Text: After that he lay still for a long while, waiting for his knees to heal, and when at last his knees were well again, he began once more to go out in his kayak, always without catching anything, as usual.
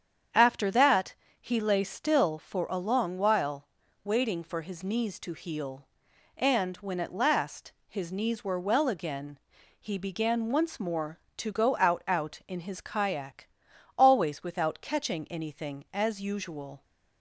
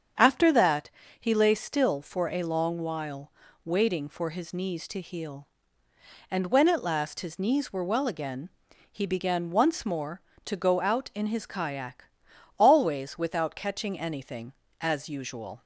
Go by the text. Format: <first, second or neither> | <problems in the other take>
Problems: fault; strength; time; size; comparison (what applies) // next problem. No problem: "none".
second | starts louder than the rest; strong; until 1.6 s; 8.5 dB; strong in the second // pauses between "that" and "he"; slight; at 1.1 s; 0.28 s long; slight in the second // pauses between "last" and "his"; slight; at 7.7 s; 0.18 s long // says "out" twice; at 12.0 s